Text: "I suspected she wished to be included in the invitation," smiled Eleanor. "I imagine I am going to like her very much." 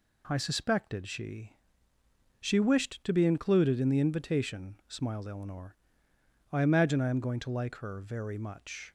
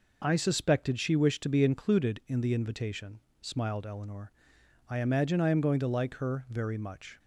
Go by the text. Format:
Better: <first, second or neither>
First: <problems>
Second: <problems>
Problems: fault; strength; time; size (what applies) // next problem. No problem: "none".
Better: second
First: says "she" twice; at 2.3 s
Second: none